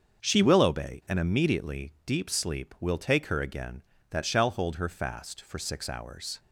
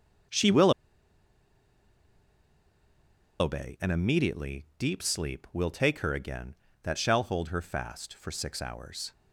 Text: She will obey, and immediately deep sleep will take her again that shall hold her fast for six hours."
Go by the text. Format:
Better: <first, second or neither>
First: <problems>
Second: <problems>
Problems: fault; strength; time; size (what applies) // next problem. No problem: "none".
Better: first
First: starts louder than the rest; until 1.3 s; 6.5 dB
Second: starts louder than the rest; until 4.0 s; 6 dB // pauses between "will" and "obey"; strong; at 0.7 s; 2.6 s long